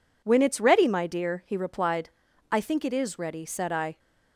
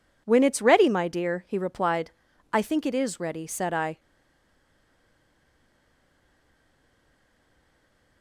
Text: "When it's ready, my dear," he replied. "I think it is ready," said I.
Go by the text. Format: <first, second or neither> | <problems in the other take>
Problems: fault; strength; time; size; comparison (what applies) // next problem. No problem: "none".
first | stays silent after the last word; strong; from 3.9 s on; 4.3 s long